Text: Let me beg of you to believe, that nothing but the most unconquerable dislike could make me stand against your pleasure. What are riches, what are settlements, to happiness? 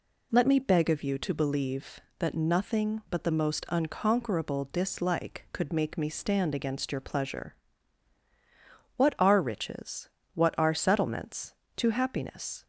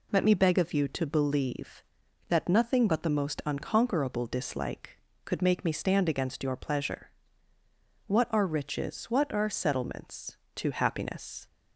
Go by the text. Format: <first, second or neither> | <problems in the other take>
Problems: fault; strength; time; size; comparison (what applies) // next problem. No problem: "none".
neither | none